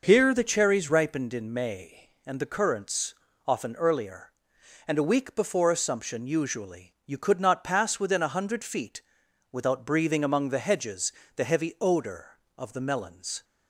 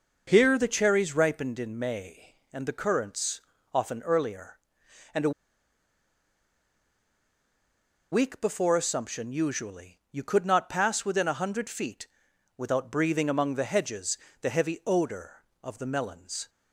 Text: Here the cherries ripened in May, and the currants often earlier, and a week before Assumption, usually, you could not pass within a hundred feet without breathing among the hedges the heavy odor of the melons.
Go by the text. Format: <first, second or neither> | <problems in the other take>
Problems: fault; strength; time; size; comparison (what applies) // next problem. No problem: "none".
first | pauses between "currants" and "often"; slight; at 3.4 s; 0.32 s long; slight in the first // pauses between "a" and "week"; strong; at 5.3 s; 2.8 s long // pauses between "feet" and "without"; noticeable; at 12.0 s; 0.50 s long; noticeable in the first // pauses between "hedges" and "the"; slight; at 14.1 s; 0.24 s long; slight in the first